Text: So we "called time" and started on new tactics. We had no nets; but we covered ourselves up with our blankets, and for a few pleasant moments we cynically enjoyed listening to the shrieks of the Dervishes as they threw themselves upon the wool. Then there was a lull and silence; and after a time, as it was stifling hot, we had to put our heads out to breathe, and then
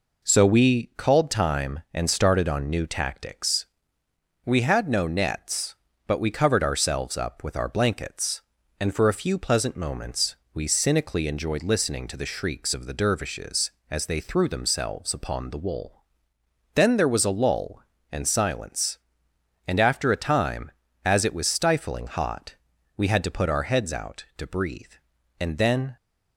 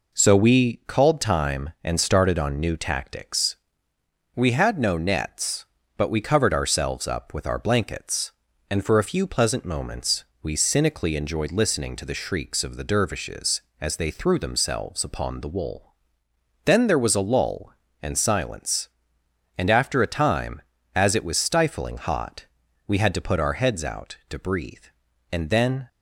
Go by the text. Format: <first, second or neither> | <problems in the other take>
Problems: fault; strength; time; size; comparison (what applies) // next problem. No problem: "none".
neither | pauses between "moments" and "we"; slight; the same in both